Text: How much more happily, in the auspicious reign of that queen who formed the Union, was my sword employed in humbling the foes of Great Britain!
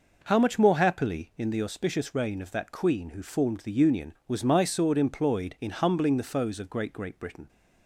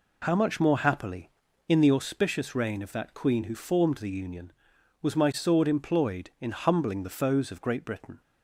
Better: second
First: says "Great" twice; at 6.9 s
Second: none

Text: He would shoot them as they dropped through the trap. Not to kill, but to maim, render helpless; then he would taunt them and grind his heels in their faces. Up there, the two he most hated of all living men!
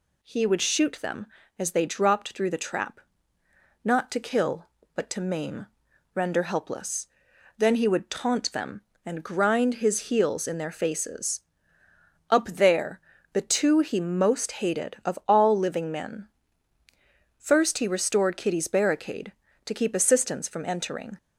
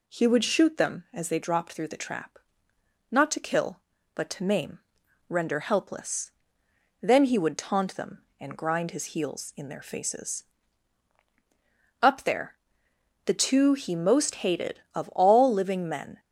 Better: second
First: goes on to say "First he restored Kitty's barricade to keep assistance from entering"; strong; from 17.3 s on; 3.7 s long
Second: none

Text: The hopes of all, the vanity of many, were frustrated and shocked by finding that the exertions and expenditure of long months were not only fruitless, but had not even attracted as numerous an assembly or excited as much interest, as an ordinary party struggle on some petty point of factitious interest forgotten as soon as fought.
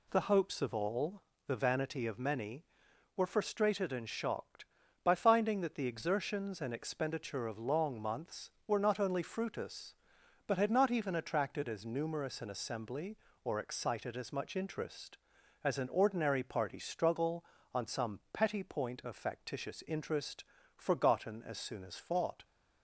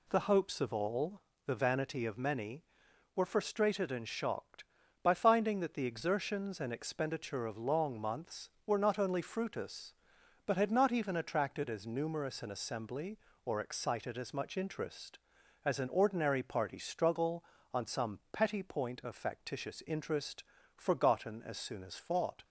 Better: neither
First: pauses between "interest" and "forgotten"; slight; at 20.4 s; 0.32 s long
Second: pauses between "interest" and "forgotten"; slight; at 20.4 s; 0.32 s long

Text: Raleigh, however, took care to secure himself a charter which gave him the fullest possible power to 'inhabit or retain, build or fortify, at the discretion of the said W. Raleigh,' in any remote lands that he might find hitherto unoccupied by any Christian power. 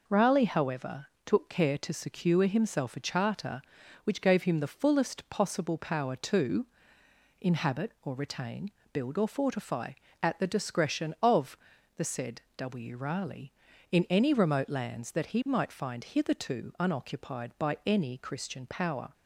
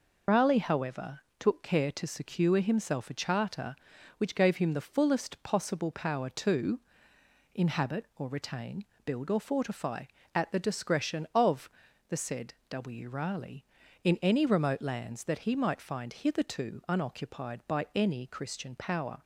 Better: first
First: pauses between "to" and "inhabit"; noticeable; at 6.6 s; 0.76 s long // pauses between "of" and "the"; at 11.5 s; 0.38 s long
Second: loses the start of "Raleigh"; at 0.2 s; 70 ms // pauses between "to" and "inhabit"; noticeable; at 6.7 s; 0.76 s long // pauses between "of" and "the"; at 11.6 s; 0.38 s long

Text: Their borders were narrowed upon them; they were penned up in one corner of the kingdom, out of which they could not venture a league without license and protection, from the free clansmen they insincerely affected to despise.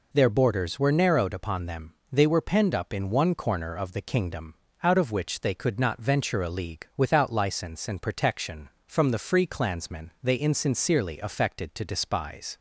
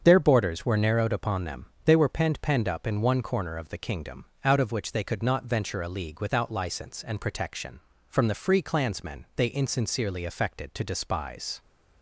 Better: first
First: none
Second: starts louder than the rest; strong; until 1.0 s; 7 dB // says "penned" twice; at 2.4 s

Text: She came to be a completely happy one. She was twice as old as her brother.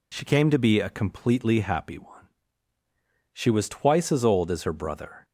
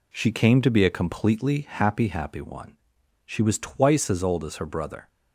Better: first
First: none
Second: says "happy" twice; at 2.0 s

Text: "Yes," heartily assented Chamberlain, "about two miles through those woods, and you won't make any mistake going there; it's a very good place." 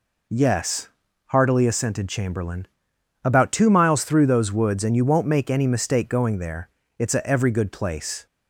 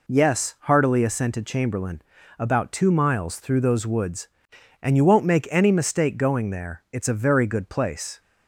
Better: second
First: says "every" for "very"; at 7.2 s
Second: none

